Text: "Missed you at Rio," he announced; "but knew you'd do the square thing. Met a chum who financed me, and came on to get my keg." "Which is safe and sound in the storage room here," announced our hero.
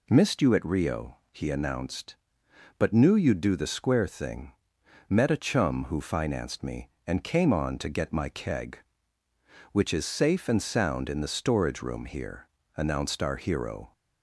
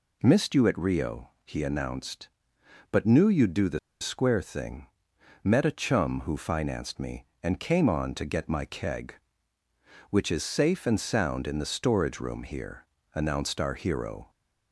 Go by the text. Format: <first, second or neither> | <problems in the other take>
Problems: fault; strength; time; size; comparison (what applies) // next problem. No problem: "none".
first | pauses between "the" and "square"; slight; at 3.7 s; 0.22 s long